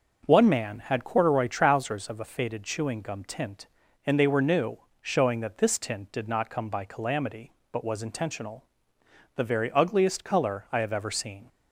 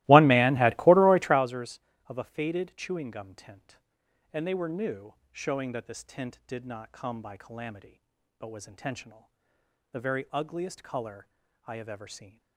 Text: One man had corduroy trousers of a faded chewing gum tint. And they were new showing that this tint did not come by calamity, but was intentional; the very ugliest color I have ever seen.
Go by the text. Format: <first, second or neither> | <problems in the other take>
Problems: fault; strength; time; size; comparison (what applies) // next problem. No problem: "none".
first | starts louder than the rest; strong; until 1.4 s; 18 dB // pauses between "new" and "showing"; slight; at 5.1 s; 0.18 s long; slight in the first // pauses between "color" and "I"; at 11.2 s; 0.42 s long